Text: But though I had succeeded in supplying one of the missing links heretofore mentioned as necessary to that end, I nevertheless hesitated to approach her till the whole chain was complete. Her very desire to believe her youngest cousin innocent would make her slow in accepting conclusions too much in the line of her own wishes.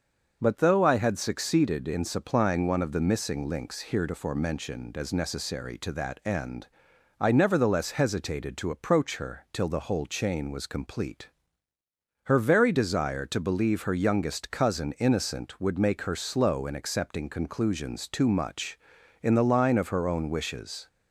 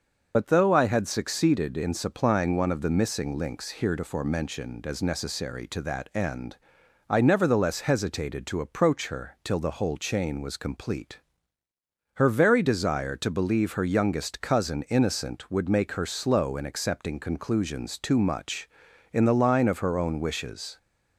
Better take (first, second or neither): first